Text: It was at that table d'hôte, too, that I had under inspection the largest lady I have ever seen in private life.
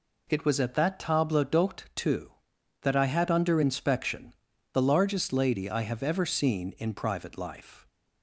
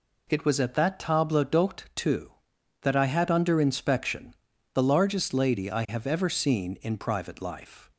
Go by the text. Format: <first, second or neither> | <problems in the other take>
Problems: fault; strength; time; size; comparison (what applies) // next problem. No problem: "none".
neither | pauses between "inspection" and "the"; the same in both